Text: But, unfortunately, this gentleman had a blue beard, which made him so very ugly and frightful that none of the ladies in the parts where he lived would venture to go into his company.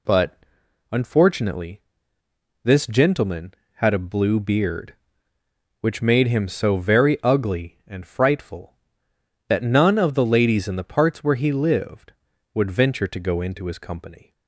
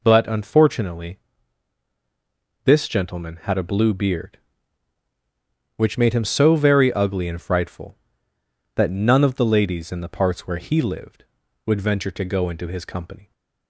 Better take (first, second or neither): neither